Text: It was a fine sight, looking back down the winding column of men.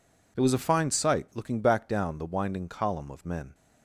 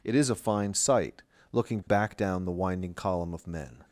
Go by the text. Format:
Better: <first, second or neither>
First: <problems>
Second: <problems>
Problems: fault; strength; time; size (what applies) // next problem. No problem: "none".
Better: first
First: none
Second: says "is" for "was"; at 0.1 s